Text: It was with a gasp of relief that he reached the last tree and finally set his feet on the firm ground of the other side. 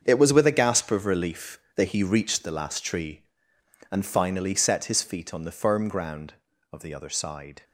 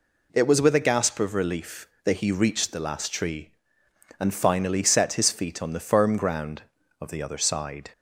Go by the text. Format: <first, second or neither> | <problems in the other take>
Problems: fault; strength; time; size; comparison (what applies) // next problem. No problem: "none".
second | gets quieter; strong; throughout; 11 dB